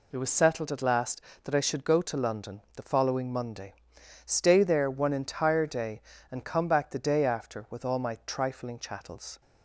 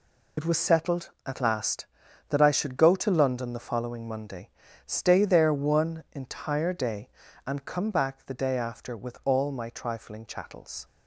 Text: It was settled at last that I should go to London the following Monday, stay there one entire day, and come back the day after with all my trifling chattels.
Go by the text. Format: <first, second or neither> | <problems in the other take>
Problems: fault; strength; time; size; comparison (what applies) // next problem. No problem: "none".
first | loses the start of "It"; at 0.3 s; 65 ms